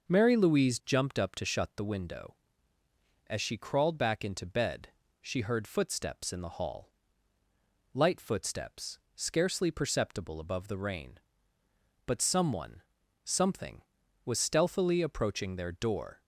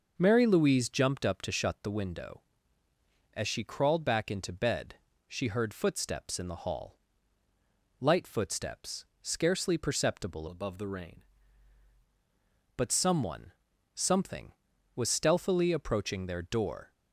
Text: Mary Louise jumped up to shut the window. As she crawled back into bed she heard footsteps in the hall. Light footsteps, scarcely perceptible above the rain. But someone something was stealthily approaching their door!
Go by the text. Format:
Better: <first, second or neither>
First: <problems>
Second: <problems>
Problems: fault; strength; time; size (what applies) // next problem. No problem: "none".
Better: first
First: pauses between "bed" and "she"; slight; at 4.8 s; 0.34 s long // pauses between "someone" and "something"; at 12.8 s; 0.42 s long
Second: pauses between "bed" and "she"; slight; at 4.9 s; 0.34 s long // changes voice from "above" to "rain"; from 10.4 to 11.2 s; 0.8 s long // pauses between "someone" and "something"; at 13.5 s; 0.42 s long